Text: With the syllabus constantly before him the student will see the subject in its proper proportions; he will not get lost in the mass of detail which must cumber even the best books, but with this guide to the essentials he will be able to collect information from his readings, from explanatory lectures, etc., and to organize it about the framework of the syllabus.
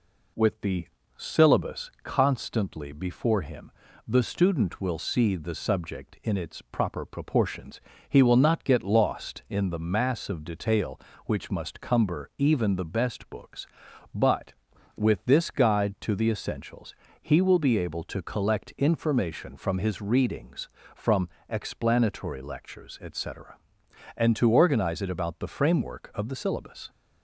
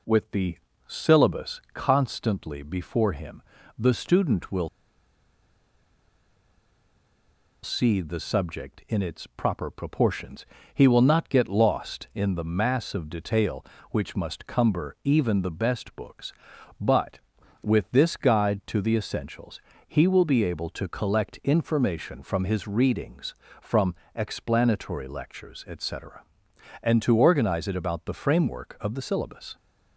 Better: first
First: pauses between "the" and "syllabus"; slight; at 0.8 s; 0.30 s long // pauses between "him" and "the"; slight; at 3.7 s; 0.34 s long // pauses between "essentials" and "he"; slight; at 16.9 s; 0.26 s long // pauses between "from" and "explanatory"; slight; at 21.2 s; 0.18 s long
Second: pauses between "the" and "syllabus"; slight; at 0.5 s; 0.30 s long // pauses between "him" and "the"; slight; at 3.4 s; 0.34 s long // pauses between "will" and "see"; strong; at 4.6 s; 2.9 s long // pauses between "essentials" and "he"; slight; at 19.6 s; 0.26 s long // pauses between "from" and "explanatory"; slight; at 23.9 s; 0.18 s long

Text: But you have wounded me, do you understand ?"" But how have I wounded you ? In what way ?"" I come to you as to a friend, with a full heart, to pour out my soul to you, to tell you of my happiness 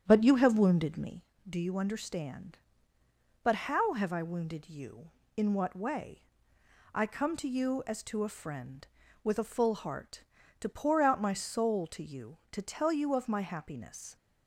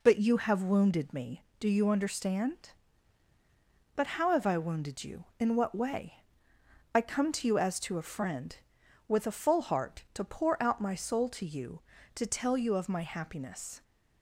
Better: second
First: starts louder than the rest; strong; until 1.3 s; 8.5 dB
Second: none

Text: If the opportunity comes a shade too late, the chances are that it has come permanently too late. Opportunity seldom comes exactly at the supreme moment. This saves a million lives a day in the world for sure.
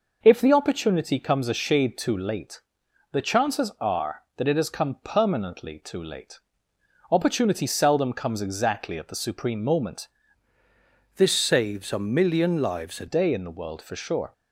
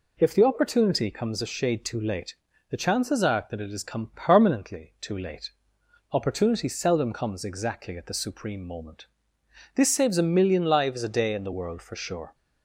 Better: second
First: changes voice from "This" to "a"; from 11.1 to 13.0 s; 1.9 s long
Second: none

